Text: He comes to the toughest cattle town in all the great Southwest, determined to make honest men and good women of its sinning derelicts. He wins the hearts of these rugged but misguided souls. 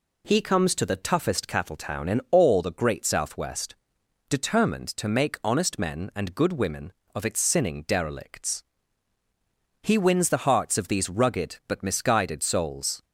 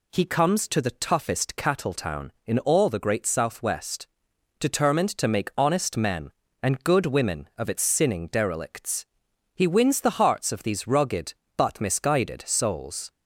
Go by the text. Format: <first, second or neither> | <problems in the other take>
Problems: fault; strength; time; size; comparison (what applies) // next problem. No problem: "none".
neither | none